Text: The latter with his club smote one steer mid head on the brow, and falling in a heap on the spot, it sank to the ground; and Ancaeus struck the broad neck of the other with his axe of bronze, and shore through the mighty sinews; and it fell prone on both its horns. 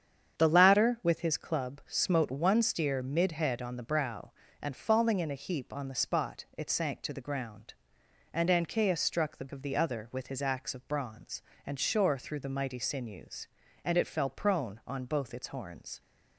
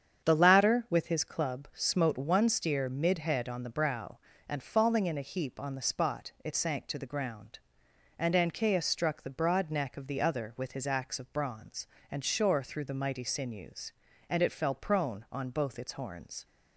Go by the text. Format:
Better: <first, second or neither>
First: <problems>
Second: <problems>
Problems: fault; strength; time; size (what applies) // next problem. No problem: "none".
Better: second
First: starts louder than the rest; strong; until 1.4 s; 8 dB // skips "broad neck"; at 9.4 s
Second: starts louder than the rest; strong; until 1.2 s; 8 dB